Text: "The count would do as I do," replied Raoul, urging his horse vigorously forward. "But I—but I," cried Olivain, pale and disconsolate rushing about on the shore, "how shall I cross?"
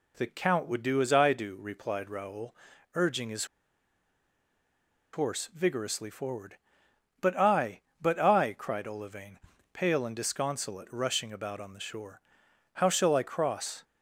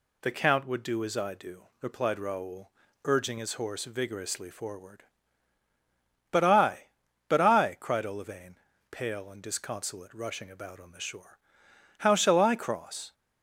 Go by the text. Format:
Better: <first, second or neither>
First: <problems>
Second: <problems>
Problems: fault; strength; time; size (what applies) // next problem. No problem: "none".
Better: second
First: pauses between "his" and "horse"; strong; at 3.4 s; 1.6 s long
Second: none